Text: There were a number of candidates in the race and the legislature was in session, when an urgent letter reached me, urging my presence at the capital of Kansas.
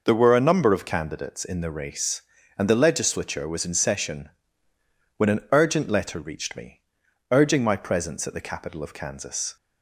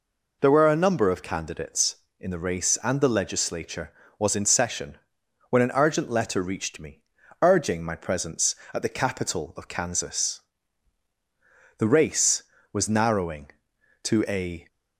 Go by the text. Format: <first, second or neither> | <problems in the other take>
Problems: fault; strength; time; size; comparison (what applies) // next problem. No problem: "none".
first | goes on to say "The race was narrowing to a"; strong; from 11.7 s on; 2.8 s long